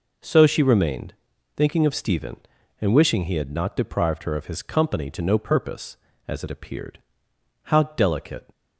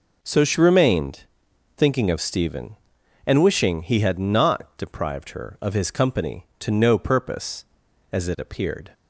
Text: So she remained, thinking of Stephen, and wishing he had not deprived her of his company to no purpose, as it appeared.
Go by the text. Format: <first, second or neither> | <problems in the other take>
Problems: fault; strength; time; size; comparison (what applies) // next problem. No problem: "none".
second | goes on to say "How delicate"; noticeable; from 7.6 s on; 0.84 s long